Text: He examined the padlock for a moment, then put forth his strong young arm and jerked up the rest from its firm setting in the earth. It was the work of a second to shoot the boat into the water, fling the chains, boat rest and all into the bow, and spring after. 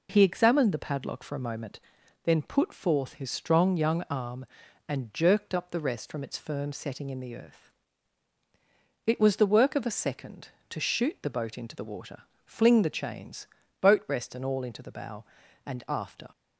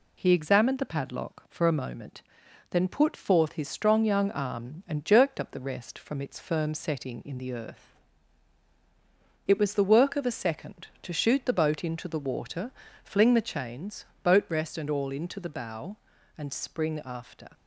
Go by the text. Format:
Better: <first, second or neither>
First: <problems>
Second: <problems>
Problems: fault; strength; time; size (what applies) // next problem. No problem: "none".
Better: second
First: skips "spring"; at 15.8 s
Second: none